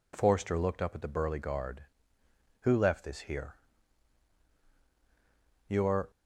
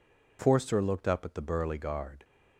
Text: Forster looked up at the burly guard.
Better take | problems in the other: second | goes on to say "Who left this here Your"; strong; from 2.6 s on; 3.5 s long

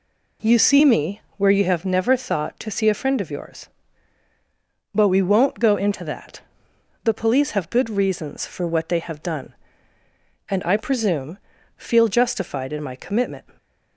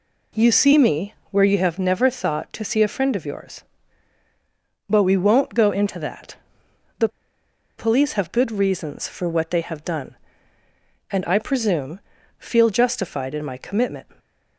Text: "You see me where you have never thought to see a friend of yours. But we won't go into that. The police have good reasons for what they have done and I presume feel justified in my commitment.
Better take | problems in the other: first | pauses between "me" and "where"; slight; at 1.1 s; 0.16 s long; slight in the first // pauses between "The" and "police"; noticeable; at 7.0 s; 0.69 s long // pauses between "presume" and "feel"; at 11.9 s; 0.40 s long; also in the first

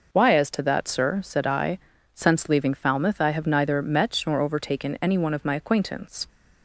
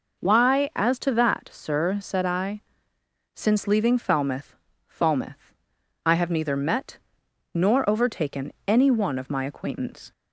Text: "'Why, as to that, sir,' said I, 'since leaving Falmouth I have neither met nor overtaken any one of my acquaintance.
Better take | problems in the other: first | says "Falmouth" twice; at 4.8 s // pauses between "met" and "nor"; noticeable; at 6.9 s; 0.56 s long

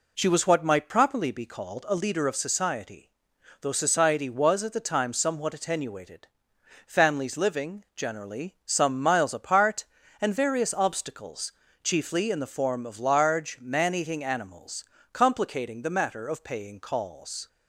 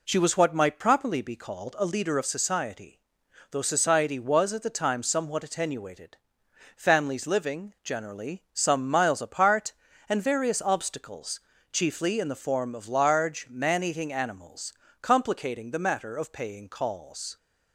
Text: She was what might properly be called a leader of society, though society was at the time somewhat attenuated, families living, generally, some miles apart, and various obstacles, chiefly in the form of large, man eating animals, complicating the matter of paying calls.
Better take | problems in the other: neither | none

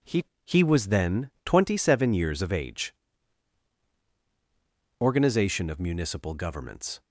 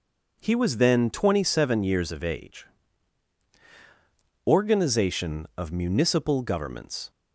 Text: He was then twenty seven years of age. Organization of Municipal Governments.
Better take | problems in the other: second | says "He" twice; at 0.4 s

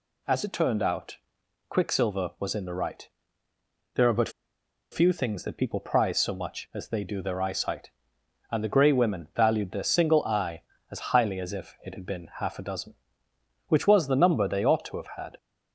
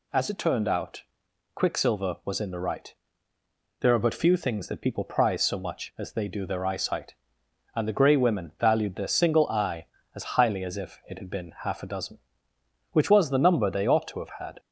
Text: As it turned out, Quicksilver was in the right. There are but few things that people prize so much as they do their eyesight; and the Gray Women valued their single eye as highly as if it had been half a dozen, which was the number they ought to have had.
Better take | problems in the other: second | pauses between "but" and "few"; noticeable; at 4.2 s; 0.62 s long

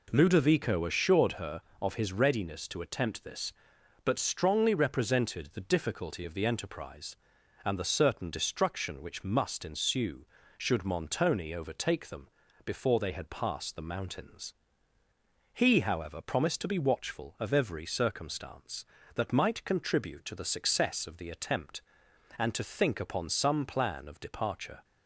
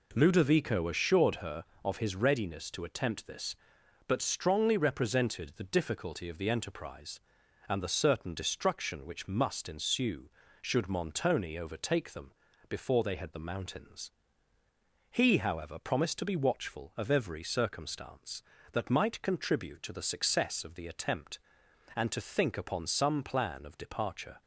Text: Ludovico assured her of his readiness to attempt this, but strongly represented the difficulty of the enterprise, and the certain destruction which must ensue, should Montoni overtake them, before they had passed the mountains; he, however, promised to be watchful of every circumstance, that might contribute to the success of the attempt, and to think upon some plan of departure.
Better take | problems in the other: first | skips "passed"; at 13.3 s

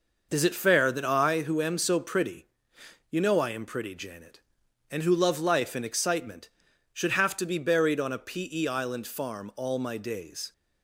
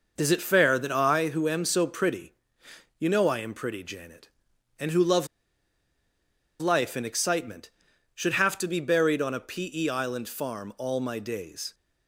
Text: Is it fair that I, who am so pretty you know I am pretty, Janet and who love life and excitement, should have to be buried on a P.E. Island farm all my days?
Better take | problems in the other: first | pauses between "pretty" and "you"; noticeable; at 2.3 s; 0.64 s long; noticeable in the first // pauses between "love" and "life"; strong; at 5.2 s; 1.3 s long

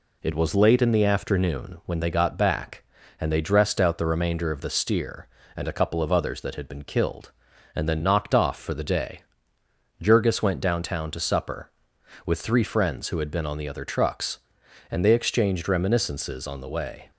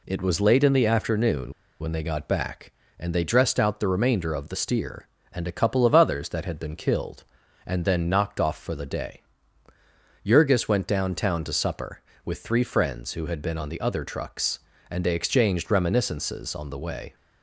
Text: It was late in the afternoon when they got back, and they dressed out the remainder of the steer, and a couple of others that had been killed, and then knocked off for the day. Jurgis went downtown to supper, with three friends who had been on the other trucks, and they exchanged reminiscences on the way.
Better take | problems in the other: first | pauses between "afternoon" and "when"; slight; at 1.5 s; 0.28 s long

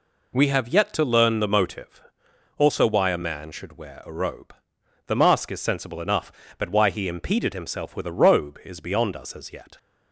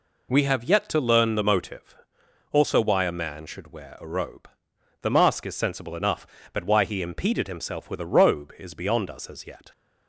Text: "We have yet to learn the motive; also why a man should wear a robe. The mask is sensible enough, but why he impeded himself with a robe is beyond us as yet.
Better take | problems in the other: neither | none

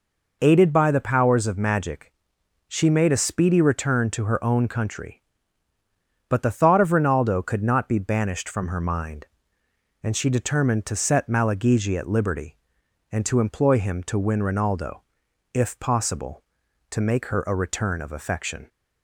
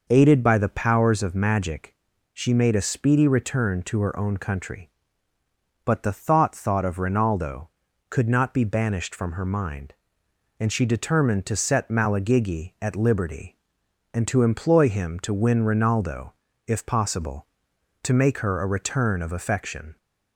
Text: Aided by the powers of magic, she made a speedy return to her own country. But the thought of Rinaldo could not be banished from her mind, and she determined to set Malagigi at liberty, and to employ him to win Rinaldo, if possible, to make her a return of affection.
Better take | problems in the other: first | says "thought" twice; at 6.5 s

